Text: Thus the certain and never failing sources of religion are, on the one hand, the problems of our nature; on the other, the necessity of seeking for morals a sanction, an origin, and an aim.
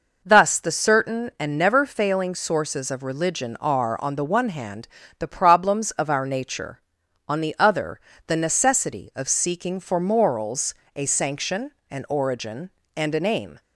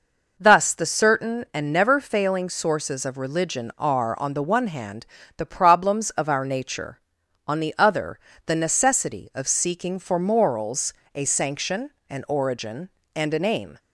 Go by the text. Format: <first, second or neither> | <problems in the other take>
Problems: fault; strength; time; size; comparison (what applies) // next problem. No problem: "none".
neither | pauses between "morals" and "a"; slight; the same in both